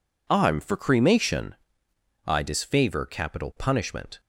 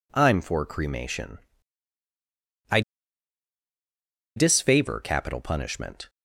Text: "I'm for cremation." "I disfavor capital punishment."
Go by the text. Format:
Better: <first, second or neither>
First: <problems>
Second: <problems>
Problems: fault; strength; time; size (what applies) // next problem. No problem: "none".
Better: first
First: none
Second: pauses between "I" and "disfavor"; strong; at 2.8 s; 1.5 s long